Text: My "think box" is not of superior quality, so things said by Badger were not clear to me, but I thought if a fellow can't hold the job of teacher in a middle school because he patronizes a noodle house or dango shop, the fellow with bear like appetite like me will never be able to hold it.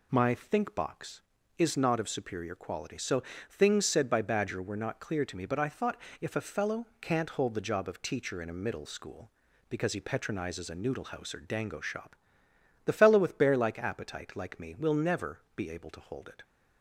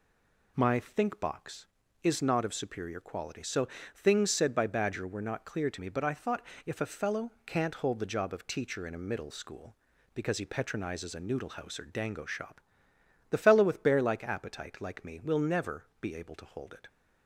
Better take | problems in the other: first | stays silent before the first word; slight; until 0.5 s; 0.5 s long // pauses between "so" and "things"; slight; at 3.6 s; 0.30 s long; slight in the first // pauses between "thought" and "if"; slight; at 6.4 s; 0.24 s long; slight in the first // pauses between "never" and "be"; slight; at 15.8 s; 0.16 s long; slight in the first

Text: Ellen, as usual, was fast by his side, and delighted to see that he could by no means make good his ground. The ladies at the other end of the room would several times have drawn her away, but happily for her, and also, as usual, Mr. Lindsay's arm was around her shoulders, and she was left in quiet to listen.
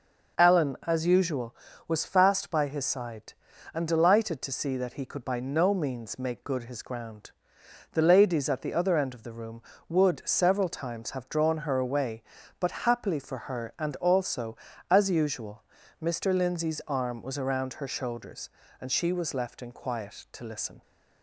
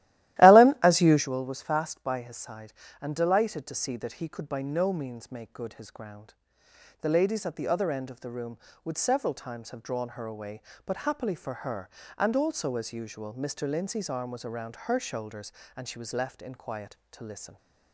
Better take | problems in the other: first | starts louder than the rest; strong; until 1.3 s; 15 dB

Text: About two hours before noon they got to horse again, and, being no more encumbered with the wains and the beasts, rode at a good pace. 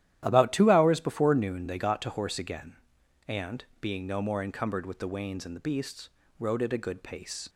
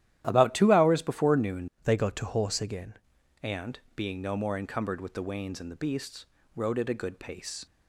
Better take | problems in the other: first | starts louder than the rest; strong; until 1.2 s; 12.5 dB; strong in the first // changes voice from "they" to "again"; from 1.8 to 2.9 s; 1.1 s long

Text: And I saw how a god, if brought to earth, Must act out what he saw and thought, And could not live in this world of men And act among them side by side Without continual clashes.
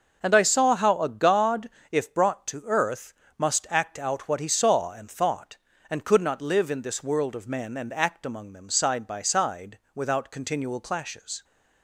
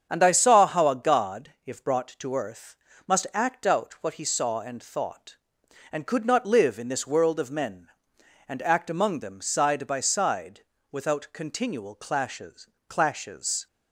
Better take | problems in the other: first | starts louder than the rest; strong; until 1.1 s; 8 dB // pauses between "side" and "Without"; slight; at 10.6 s; 0.30 s long; slight in the first // says "clashes" twice; at 12.8 s

